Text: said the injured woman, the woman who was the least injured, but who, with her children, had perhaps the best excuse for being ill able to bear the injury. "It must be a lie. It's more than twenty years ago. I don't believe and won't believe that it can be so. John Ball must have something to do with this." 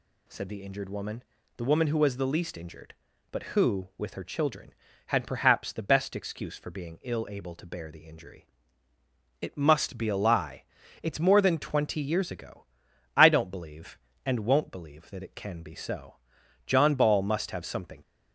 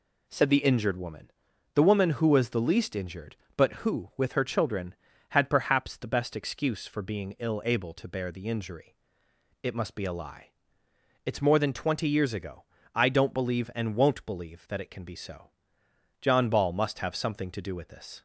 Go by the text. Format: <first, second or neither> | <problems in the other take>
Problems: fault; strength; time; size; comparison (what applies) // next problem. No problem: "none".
second | stops before "to do with this"; at 18.0 s